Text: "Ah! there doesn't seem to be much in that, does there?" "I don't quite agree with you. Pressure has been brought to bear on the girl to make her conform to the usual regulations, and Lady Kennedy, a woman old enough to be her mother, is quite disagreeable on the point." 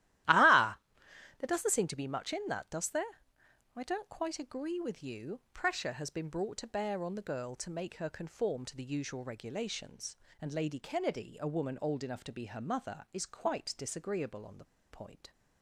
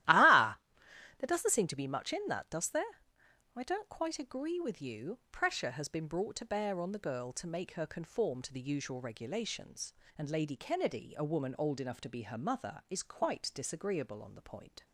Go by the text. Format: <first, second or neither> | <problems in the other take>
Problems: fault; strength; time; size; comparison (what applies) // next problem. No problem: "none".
second | starts louder than the rest; strong; until 1.8 s; 14.5 dB; strong in the second // pauses between "the" and "point"; slight; at 14.6 s; 0.26 s long